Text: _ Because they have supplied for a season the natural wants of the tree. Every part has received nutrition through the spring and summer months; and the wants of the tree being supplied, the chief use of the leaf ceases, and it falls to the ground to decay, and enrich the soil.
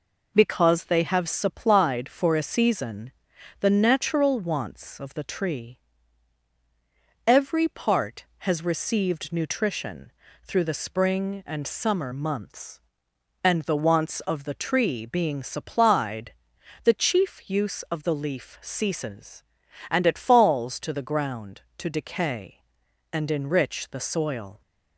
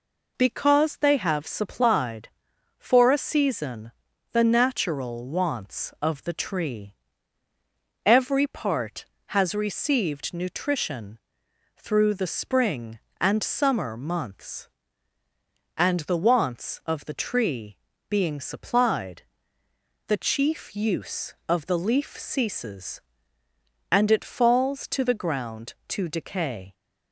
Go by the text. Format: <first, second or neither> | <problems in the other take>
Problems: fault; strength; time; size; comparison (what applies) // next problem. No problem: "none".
first | pauses between "season" and "the"; at 3.9 s; 0.42 s long; noticeable in the first // pauses between "nutrition" and "through"; noticeable; at 11.1 s; 0.58 s long; slight in the first // pauses between "tree" and "being"; slight; at 17.7 s; 0.32 s long // stops before "and enrich the soil"; at 26.7 s